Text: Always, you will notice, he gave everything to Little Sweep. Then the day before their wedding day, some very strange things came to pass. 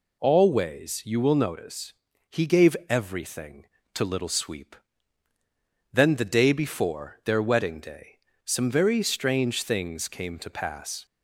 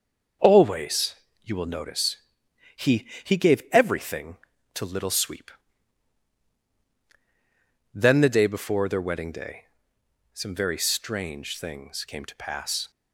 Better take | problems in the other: first | starts louder than the rest; until 1.6 s; 6.5 dB // says "he" twice; at 3.2 s

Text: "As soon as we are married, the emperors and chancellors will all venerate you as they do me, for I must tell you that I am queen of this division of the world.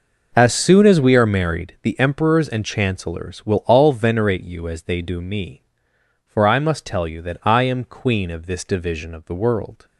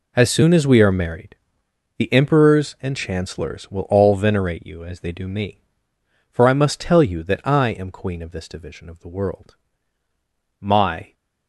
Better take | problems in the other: first | goes on to say "My"; from 10.6 s on; 0.52 s long

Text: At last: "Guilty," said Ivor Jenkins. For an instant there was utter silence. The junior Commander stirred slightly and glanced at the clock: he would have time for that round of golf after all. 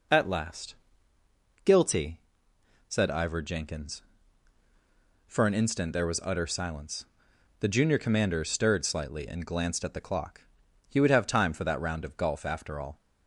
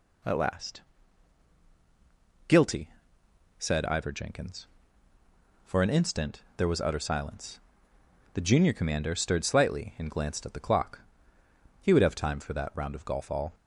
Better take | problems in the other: first | pauses between "instant" and "there"; slight; at 6.4 s; 0.16 s long // skips "after"; at 13.3 s

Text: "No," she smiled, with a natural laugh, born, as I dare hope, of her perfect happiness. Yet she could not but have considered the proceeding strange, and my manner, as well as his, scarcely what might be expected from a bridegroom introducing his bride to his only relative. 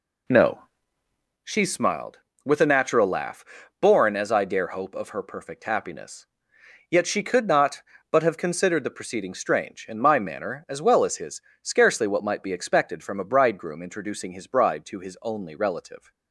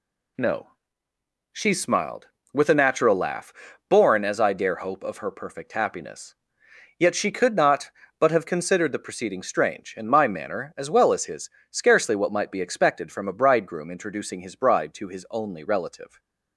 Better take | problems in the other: second | starts louder than the rest; slight; until 1.5 s; 2.5 dB

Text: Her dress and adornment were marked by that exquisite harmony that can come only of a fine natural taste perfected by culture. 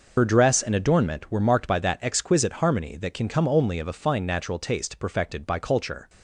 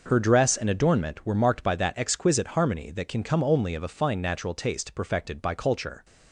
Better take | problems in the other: second | loses the start of "Her"; at 0.1 s; 60 ms

